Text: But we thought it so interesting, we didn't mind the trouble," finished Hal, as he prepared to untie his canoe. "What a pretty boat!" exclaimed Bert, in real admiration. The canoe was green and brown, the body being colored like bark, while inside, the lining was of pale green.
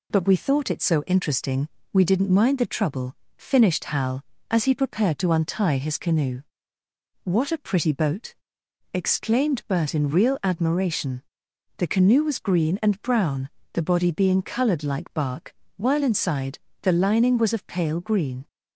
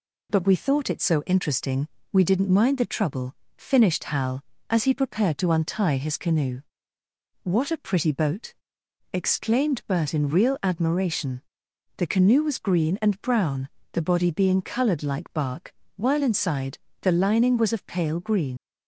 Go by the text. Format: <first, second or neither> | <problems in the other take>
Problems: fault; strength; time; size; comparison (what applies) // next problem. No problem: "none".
first | leaves "green" unfinished; at 18.5 s; 95 ms